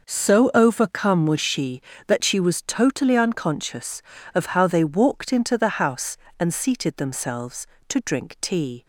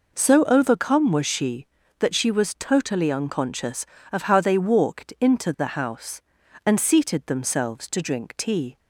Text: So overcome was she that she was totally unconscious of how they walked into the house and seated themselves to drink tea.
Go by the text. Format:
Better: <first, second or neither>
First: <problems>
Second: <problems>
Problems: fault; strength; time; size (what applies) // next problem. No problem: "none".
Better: neither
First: none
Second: none